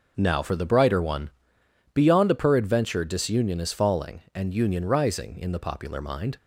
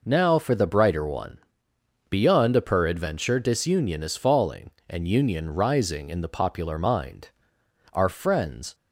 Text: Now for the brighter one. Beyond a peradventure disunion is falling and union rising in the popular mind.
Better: first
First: none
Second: goes on to say "Our friends"; noticeable; from 7.9 s on; 0.82 s long

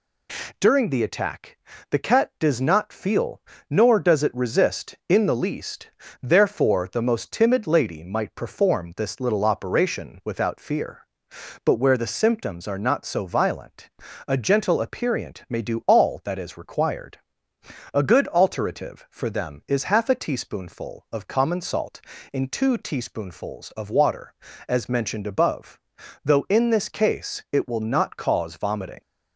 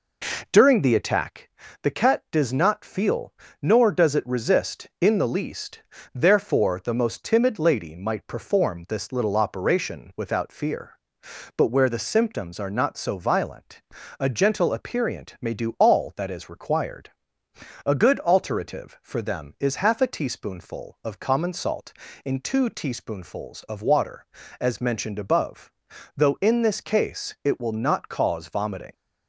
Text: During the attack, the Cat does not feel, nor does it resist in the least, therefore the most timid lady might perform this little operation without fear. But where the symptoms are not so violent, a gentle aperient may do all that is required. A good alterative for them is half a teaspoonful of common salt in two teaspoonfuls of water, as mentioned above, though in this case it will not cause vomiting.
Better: first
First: none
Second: starts louder than the rest; noticeable; until 1.4 s; 4 dB

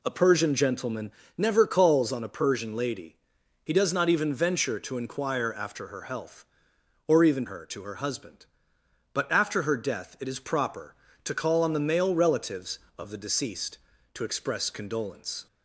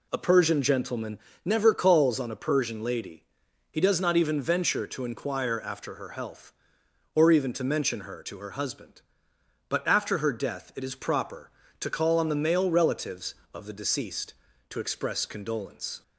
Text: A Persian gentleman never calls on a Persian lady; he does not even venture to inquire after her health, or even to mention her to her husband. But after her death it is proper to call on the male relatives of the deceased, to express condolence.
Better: second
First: pauses between "gentleman" and "never"; slight; at 1.1 s; 0.26 s long // skips "to mention"; at 7.4 s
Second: pauses between "gentleman" and "never"; slight; at 1.1 s; 0.26 s long

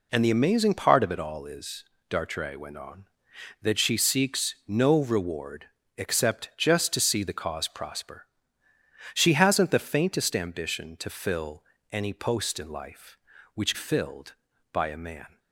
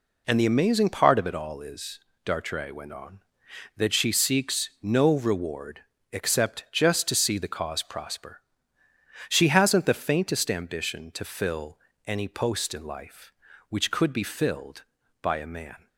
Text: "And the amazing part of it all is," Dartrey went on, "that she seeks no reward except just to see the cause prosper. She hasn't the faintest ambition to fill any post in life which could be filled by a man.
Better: second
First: pauses between "reward" and "except"; slight; at 5.6 s; 0.30 s long // pauses between "fill" and "any"; slight; at 11.6 s; 0.28 s long // skips "could be"; at 13.7 s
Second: pauses between "reward" and "except"; slight; at 5.8 s; 0.30 s long // pauses between "fill" and "any"; slight; at 11.7 s; 0.28 s long

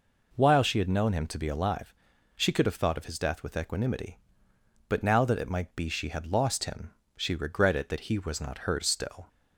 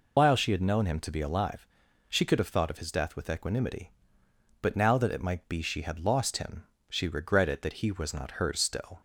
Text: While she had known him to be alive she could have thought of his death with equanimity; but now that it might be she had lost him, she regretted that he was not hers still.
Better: first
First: pauses between "alive" and "she"; at 1.9 s; 0.42 s long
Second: loses the start of "While"; at 0.1 s; 120 ms // pauses between "alive" and "she"; at 1.6 s; 0.42 s long

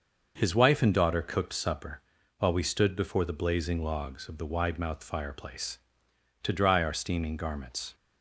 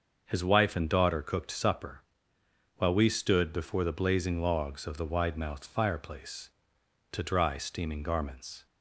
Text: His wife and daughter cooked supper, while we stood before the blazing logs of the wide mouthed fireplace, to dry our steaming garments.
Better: first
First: starts louder than the rest; noticeable; until 1.3 s; 6 dB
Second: starts louder than the rest; until 1.2 s; 6.5 dB // skips "our"; at 7.5 s

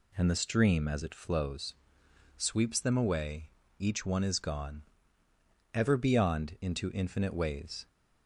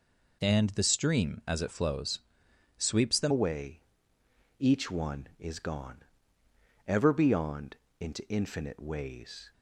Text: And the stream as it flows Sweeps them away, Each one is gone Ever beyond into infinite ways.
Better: first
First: pauses between "flows" and "Sweeps"; noticeable; at 1.7 s; 0.62 s long // pauses between "gone" and "Ever"; noticeable; at 4.8 s; 0.90 s long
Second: pauses between "flows" and "Sweeps"; noticeable; at 2.2 s; 0.56 s long // changes voice at "away"; from 3.3 s on; 6.2 s long // pauses between "gone" and "Ever"; noticeable; at 6.0 s; 0.84 s long // pauses between "beyond" and "into"; slight; at 7.7 s; 0.24 s long

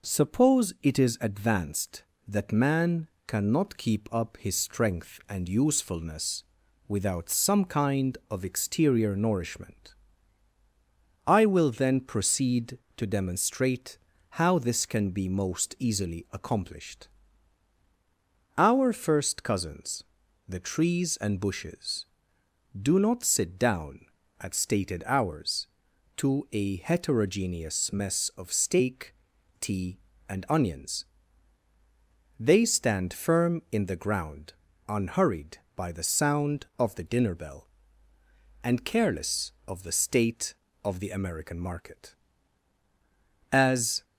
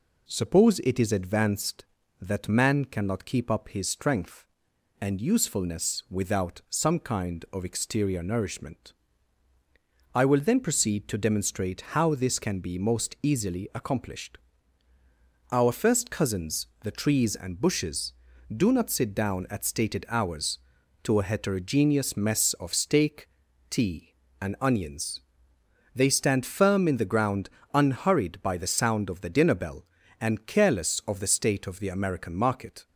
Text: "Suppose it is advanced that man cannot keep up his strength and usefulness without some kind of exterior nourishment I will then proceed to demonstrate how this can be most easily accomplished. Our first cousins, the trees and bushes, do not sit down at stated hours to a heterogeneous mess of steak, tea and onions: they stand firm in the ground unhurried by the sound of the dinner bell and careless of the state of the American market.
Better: second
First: pauses between "man" and "cannot"; slight; at 3.0 s; 0.20 s long // pauses between "usefulness" and "without"; at 6.4 s; 0.44 s long // pauses between "nourishment" and "I"; strong; at 9.9 s; 1.3 s long // pauses between "demonstrate" and "how"; slight; at 13.9 s; 0.32 s long // pauses between "ground" and "unhurried"; slight; at 34.5 s; 0.34 s long // goes on to say "As"; from 43.5 s on; 0.54 s long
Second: pauses between "nourishment" and "I"; at 8.9 s; 1.2 s long // pauses between "ground" and "unhurried"; slight; at 27.4 s; 0.24 s long

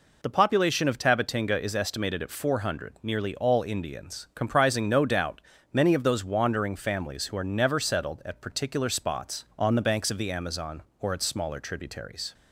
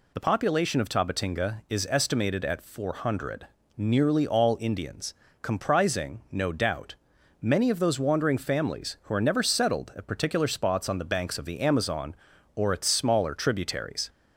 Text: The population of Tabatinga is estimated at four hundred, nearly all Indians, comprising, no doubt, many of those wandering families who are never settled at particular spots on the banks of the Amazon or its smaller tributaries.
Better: neither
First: none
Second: none

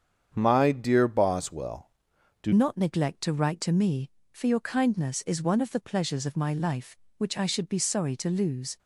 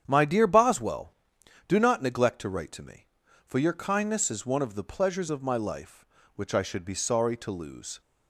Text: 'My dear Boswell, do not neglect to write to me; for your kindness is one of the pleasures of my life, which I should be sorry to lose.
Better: second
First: starts louder than the rest; strong; until 1.3 s; 8 dB // changes voice at "not"; from 2.5 s on; 6.2 s long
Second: starts louder than the rest; strong; until 1.0 s; 9 dB

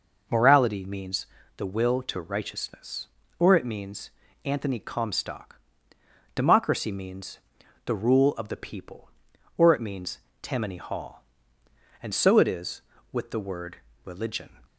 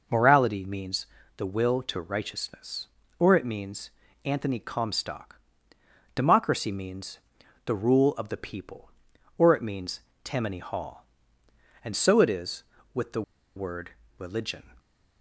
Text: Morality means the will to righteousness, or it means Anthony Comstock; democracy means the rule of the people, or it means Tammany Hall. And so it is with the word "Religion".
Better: first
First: pauses between "means" and "the"; slight; at 1.2 s; 0.30 s long // pauses between "means" and "Anthony"; slight; at 4.0 s; 0.34 s long // pauses between "means" and "the"; noticeable; at 7.3 s; 0.48 s long // pauses between "means" and "Tammany"; slight; at 10.1 s; 0.22 s long // pauses between "word" and "Religion"; slight; at 13.7 s; 0.26 s long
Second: pauses between "means" and "the"; slight; at 1.0 s; 0.30 s long // pauses between "means" and "Anthony"; slight; at 3.8 s; 0.34 s long // pauses between "means" and "the"; noticeable; at 7.1 s; 0.48 s long // pauses between "means" and "Tammany"; slight; at 10.0 s; 0.22 s long // pauses between "the" and "word"; slight; at 13.2 s; 0.34 s long // pauses between "word" and "Religion"; slight; at 13.9 s; 0.26 s long

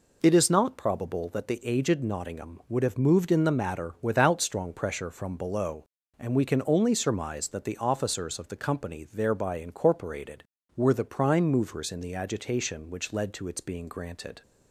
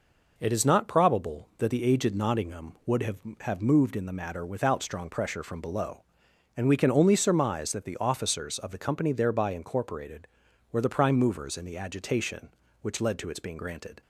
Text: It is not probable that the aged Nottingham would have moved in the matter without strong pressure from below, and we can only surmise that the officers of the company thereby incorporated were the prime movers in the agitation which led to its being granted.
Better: first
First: none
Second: says "have" twice; at 3.4 s

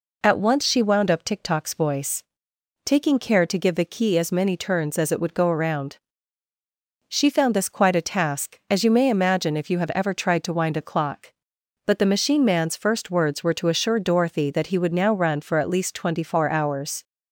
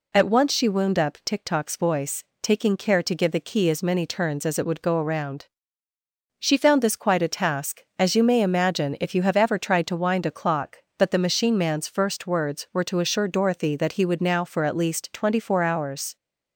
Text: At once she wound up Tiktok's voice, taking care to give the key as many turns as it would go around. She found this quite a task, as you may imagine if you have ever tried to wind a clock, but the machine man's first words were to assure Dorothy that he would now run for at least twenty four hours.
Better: first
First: none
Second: skips "run"; at 14.4 s

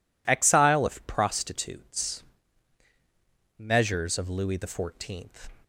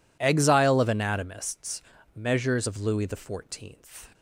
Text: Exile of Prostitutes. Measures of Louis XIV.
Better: first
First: none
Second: says "Anatomists" for "Prostitutes"; at 0.8 s

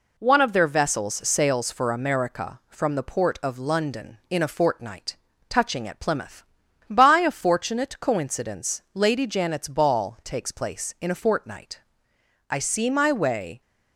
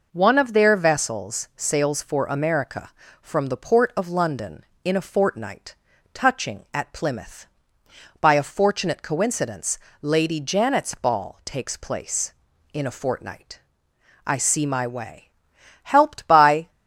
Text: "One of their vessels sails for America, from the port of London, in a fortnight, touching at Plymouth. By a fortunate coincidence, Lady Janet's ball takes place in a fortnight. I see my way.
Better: first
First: none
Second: goes on to say "Helped by"; noticeable; from 15.8 s on; 0.86 s long

